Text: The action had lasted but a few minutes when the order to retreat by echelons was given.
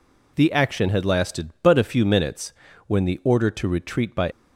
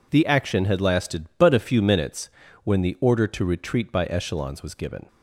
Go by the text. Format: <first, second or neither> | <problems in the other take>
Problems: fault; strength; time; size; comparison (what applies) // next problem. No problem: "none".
second | pauses between "minutes" and "when"; slight; at 2.5 s; 0.34 s long; slight in the second // stops before "echelons was given"; at 4.3 s